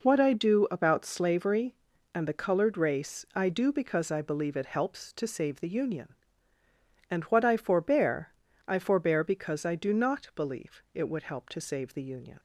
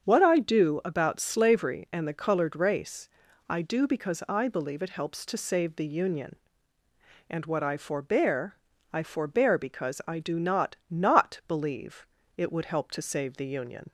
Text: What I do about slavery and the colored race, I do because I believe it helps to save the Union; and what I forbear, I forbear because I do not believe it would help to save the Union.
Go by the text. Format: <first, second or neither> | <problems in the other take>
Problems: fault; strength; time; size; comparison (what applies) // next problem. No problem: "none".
first | starts louder than the rest; strong; until 1.0 s; 7 dB // says "not" twice; at 10.8 s // pauses between "believe" and "it"; slight; at 12.0 s; 0.30 s long